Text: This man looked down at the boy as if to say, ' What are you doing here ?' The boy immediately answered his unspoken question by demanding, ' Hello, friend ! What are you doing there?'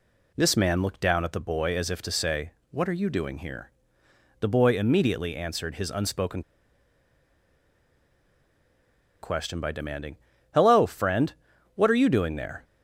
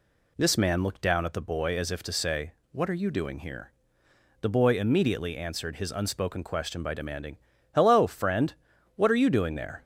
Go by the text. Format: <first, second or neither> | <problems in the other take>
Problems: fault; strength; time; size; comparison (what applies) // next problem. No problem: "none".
second | pauses between "unspoken" and "question"; strong; at 6.4 s; 2.8 s long